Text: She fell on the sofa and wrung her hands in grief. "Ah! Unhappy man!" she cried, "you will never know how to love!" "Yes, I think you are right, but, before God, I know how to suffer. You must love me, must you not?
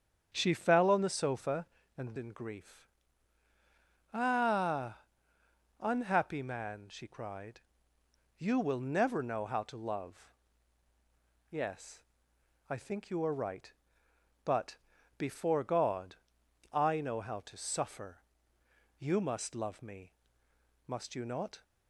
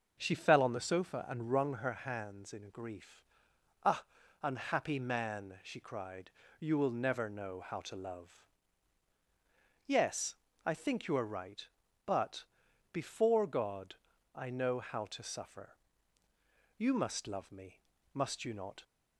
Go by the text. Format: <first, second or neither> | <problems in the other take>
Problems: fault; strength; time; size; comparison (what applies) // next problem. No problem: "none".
second | starts louder than the rest; strong; until 1.3 s; 8 dB // skips "wrung her hands"; at 2.1 s